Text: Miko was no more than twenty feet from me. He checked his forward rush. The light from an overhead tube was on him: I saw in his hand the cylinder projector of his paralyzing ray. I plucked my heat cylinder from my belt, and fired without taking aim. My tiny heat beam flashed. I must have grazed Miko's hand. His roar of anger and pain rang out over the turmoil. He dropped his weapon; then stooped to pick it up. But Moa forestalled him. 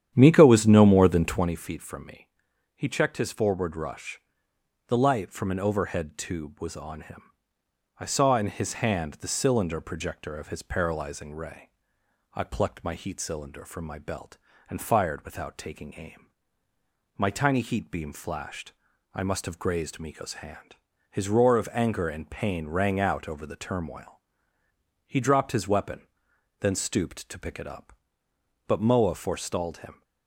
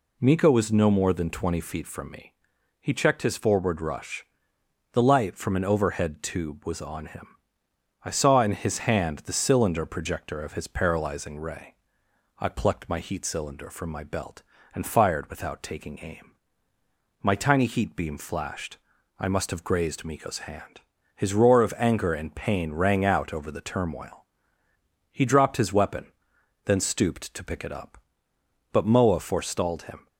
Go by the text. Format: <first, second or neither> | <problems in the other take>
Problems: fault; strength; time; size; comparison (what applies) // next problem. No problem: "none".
second | starts louder than the rest; strong; until 1.5 s; 10 dB